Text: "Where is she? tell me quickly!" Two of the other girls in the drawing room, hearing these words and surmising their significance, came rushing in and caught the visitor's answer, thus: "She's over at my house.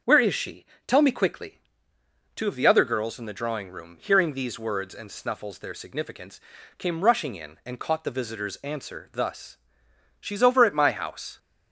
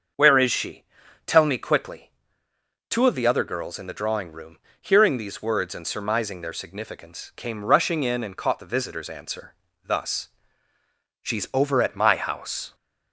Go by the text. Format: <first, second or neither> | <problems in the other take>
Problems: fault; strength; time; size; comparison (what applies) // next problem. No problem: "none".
second | starts louder than the rest; until 1.2 s; 6.5 dB; also in the second // says "snuffles" for "surmising"; at 5.0 s